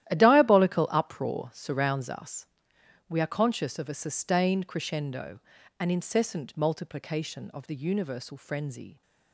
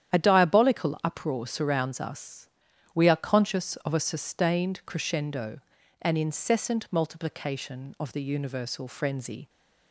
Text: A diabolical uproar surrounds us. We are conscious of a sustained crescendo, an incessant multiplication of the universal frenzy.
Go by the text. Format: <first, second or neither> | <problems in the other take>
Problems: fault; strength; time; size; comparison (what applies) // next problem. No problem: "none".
second | gets quieter; strong; throughout; 14 dB // starts louder than the rest; strong; until 1.1 s; 12.5 dB; strong in the second